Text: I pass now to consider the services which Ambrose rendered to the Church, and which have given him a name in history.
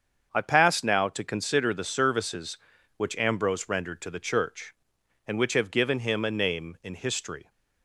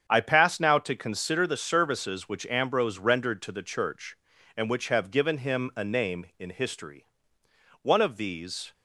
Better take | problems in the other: first | starts louder than the rest; strong; until 1.1 s; 8 dB; also in the first // goes on to say "One of these"; noticeable; from 7.8 s on; 0.92 s long

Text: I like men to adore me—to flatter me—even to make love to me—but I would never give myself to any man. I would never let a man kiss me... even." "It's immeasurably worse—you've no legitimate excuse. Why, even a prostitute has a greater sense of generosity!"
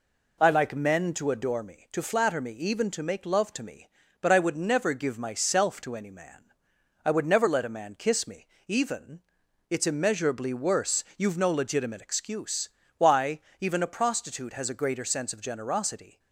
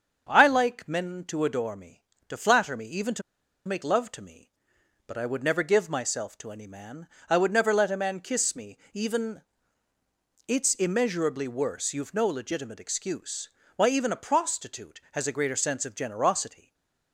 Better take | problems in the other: first | starts louder than the rest; until 1.3 s; 7 dB // pauses between "to" and "make"; at 3.2 s; 0.45 s long // stays silent after the last word; slight; from 16.5 s on; 0.6 s long

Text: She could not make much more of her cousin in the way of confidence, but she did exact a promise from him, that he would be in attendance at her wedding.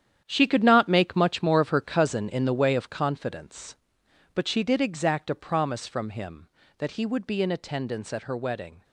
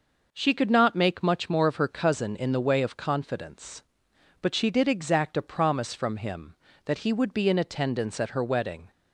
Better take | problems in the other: second | gets quieter; strong; throughout; 11 dB

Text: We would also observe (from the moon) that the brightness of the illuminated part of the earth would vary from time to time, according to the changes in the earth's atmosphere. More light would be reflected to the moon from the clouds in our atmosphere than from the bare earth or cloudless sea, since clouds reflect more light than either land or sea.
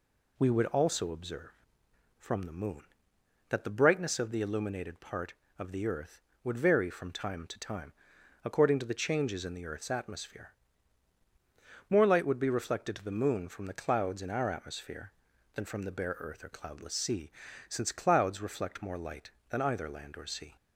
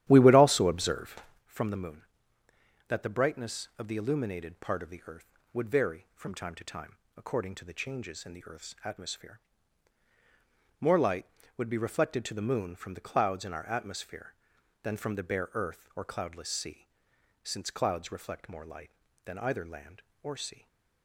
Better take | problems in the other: first | starts louder than the rest; strong; until 1.5 s; 12 dB // stays silent after the last word; slight; from 20.5 s on; 0.5 s long

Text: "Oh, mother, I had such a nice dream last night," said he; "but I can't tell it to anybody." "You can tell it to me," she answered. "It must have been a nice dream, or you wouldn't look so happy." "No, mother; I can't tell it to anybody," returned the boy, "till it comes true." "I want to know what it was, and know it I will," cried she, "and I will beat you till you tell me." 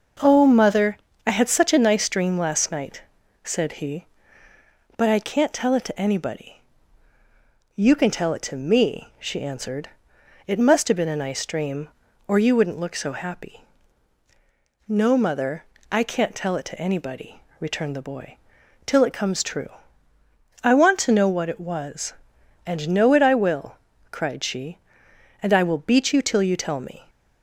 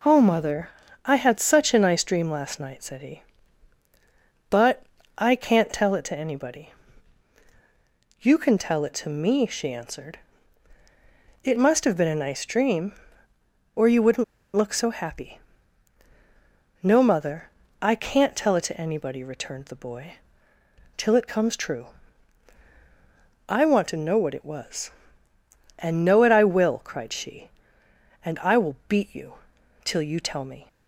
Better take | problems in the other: first | pauses between "but" and "I"; slight; at 4.8 s; 0.32 s long // pauses between "wouldn't" and "look"; slight; at 14.2 s; 0.31 s long // pauses between "you" and "till"; noticeable; at 29.3 s; 0.50 s long

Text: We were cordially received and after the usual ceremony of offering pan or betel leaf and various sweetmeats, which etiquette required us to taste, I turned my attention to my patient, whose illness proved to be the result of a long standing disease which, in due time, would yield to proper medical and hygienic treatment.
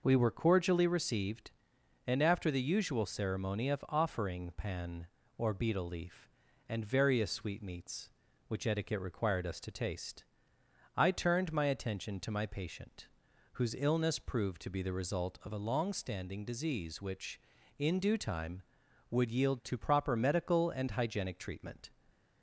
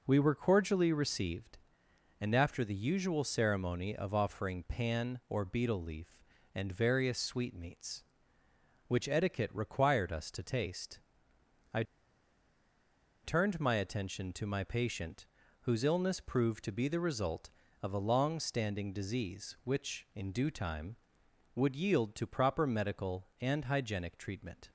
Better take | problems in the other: first | pauses between "I" and "turned"; strong; at 11.8 s; 1.4 s long

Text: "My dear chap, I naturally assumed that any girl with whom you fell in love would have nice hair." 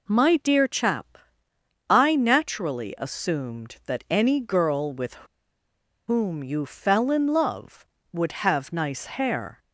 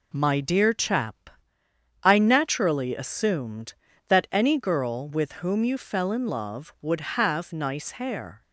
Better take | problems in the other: second | pauses between "with" and "whom"; noticeable; at 5.1 s; 0.94 s long

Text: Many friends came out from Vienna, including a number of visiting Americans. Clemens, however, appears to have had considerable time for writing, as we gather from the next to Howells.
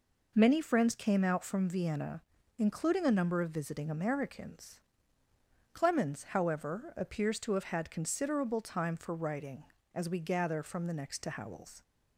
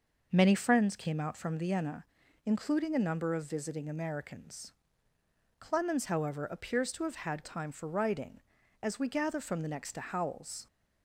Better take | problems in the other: first | skips "considerable"; at 7.4 s

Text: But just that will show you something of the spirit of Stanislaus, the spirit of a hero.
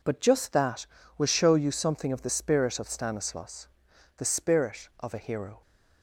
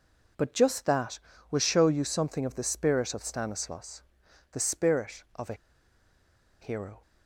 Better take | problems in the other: first | pauses between "a" and "hero"; at 5.5 s; 1.0 s long

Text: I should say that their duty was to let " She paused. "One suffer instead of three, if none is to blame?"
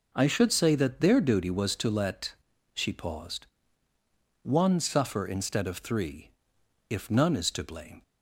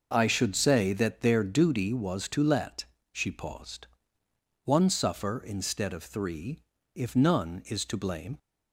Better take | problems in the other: neither | none

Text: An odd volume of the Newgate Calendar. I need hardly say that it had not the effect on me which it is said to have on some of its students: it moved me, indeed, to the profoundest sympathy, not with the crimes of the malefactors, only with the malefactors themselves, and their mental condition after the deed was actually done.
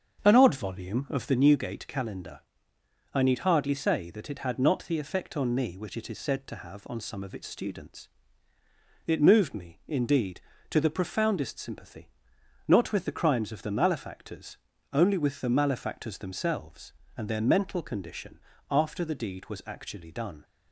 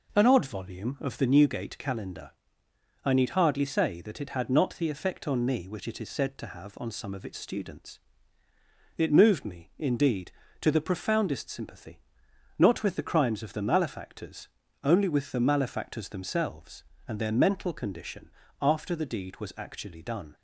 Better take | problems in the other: second | starts louder than the rest; strong; until 1.4 s; 7 dB // pauses between "condition" and "after"; slight; at 18.3 s; 0.30 s long; slight in the second

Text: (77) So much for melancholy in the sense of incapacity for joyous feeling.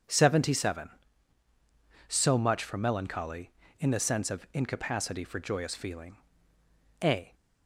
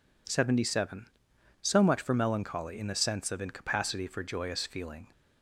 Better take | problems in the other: second | goes on to say "A"; slight; from 7.0 s on; 0.32 s long

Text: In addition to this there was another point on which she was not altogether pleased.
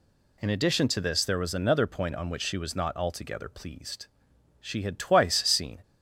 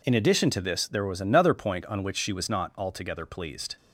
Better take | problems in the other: second | goes on to say "She had twice seen"; noticeable; from 4.6 s on; 1.2 s long

